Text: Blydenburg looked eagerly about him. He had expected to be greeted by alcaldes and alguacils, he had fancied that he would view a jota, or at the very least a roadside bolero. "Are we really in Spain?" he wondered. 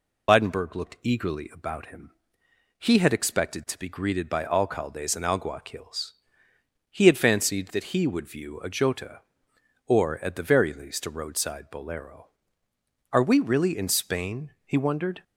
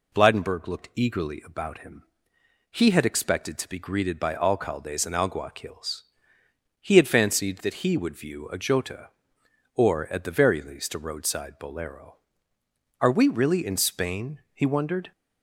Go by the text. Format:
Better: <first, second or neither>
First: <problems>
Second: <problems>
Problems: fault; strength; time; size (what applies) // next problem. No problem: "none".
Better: second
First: loses the start of "Blydenburg"; at 0.2 s; 75 ms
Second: none